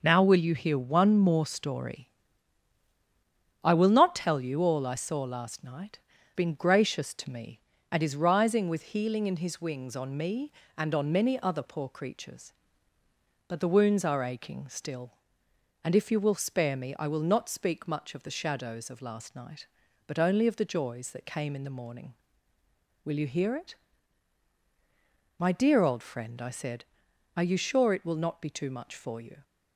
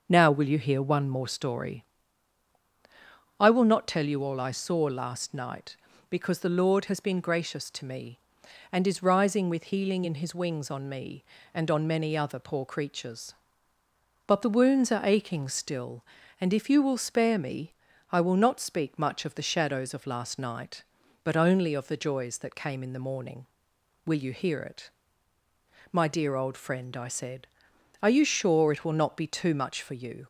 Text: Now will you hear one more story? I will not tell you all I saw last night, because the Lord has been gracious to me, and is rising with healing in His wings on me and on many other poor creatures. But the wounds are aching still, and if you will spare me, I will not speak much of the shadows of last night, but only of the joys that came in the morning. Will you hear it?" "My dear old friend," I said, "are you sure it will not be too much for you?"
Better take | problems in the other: second | starts louder than the rest; noticeable; until 1.0 s; 6 dB; also in the second // skips "because the Lord has"; at 6.1 s

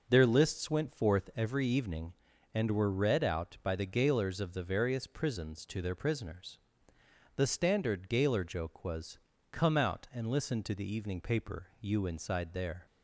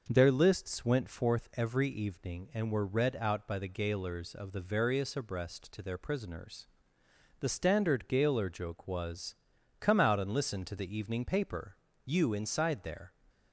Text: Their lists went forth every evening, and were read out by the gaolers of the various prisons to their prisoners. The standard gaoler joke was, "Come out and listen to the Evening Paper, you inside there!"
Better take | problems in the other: first | says "abreast" for "prisons"; at 5.1 s

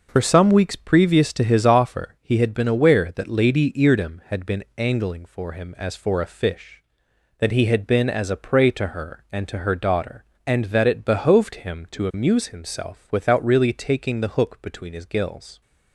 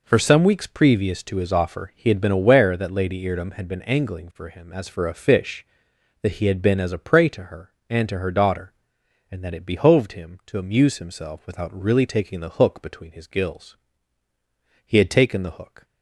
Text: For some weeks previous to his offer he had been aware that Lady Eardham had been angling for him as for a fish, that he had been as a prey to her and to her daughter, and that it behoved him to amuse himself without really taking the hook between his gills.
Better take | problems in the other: first | goes on to say "He had taken the hook"; noticeable; from 14.8 s on; 0.98 s long

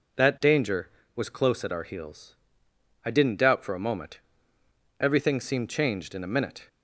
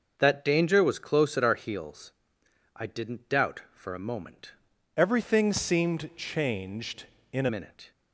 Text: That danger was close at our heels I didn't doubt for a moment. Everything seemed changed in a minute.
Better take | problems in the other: first | starts louder than the rest; noticeable; until 1.1 s; 6 dB // pauses between "heels" and "I"; noticeable; at 2.1 s; 0.64 s long; noticeable in the first // changes voice from "Everything" to "a"; from 4.9 to 7.4 s; 2.5 s long

